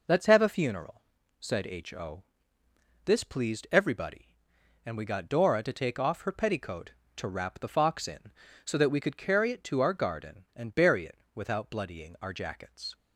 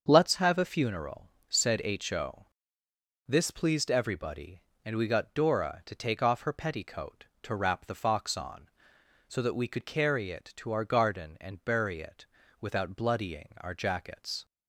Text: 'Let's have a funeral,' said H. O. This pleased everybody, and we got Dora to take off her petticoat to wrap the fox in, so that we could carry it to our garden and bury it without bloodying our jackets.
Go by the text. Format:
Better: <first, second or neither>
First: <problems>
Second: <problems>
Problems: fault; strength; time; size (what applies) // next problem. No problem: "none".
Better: first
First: pauses between "O" and "This"; noticeable; at 2.2 s; 0.82 s long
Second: starts louder than the rest; until 1.0 s; 6.5 dB // pauses between "O" and "This"; noticeable; at 2.4 s; 0.82 s long // says "on" for "in"; at 8.3 s // pauses between "it" and "without"; slight; at 12.2 s; 0.36 s long